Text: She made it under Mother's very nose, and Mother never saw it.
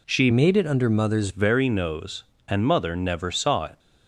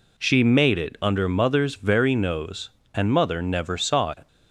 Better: second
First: changes voice from "made" to "Mother's"; from 0.3 to 1.2 s; 0.9 s long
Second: none

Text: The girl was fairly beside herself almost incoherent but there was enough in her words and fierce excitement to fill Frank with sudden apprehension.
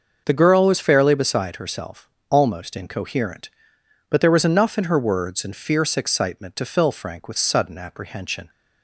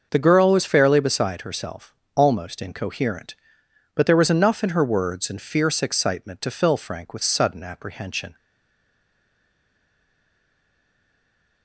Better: first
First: starts louder than the rest; noticeable; until 1.2 s; 6 dB // pauses between "herself" and "almost"; slight; at 2.0 s; 0.22 s long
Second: starts louder than the rest; noticeable; until 1.1 s; 6 dB // pauses between "herself" and "almost"; slight; at 1.9 s; 0.22 s long // stays silent after the last word; strong; from 8.3 s on; 3.3 s long

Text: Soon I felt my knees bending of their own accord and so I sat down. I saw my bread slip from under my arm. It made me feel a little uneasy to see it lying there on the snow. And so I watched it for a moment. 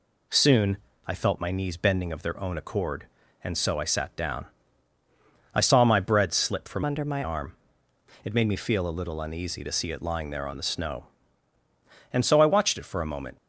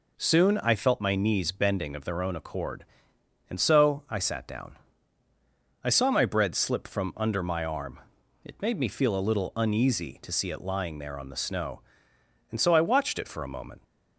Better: second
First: pauses between "Soon" and "I"; slight; at 0.7 s; 0.30 s long // changes voice from "under" to "my"; from 6.8 to 7.2 s; 0.4 s long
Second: none

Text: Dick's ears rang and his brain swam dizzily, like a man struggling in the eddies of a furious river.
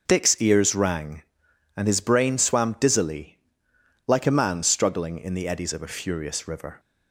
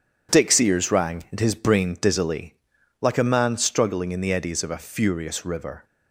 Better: first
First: none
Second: skips "swam"; at 1.9 s

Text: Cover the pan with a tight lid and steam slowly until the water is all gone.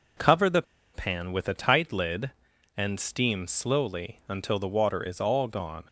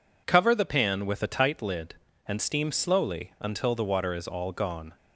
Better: second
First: pauses between "the" and "pan"; slight; at 0.6 s; 0.31 s long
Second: none

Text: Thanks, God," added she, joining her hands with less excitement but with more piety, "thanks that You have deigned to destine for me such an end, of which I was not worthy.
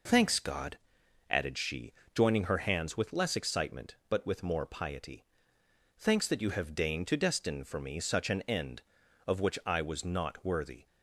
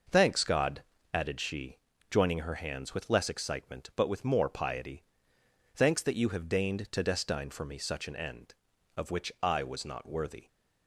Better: neither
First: none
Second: none

